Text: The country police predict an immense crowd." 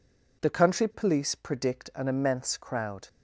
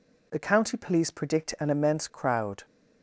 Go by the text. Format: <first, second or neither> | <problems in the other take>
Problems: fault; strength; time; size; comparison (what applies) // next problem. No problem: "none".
first | says "county" for "country"; at 0.3 s